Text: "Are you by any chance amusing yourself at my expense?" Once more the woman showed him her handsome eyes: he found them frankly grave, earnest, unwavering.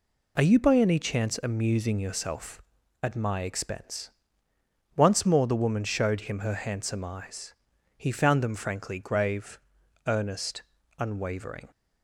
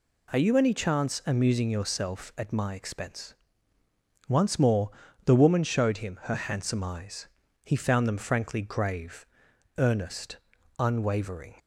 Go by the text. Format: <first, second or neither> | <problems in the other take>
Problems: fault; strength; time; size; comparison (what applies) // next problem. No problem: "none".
first | skips "by"; at 0.5 s // pauses between "more" and "the"; slight; at 4.9 s; 0.34 s long